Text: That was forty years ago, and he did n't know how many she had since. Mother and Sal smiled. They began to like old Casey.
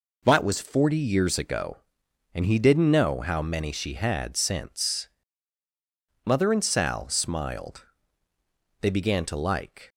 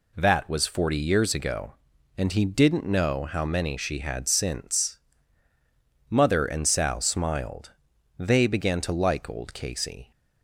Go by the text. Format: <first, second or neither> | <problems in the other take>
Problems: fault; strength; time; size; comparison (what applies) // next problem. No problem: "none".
second | stops before "old Casey"; at 9.8 s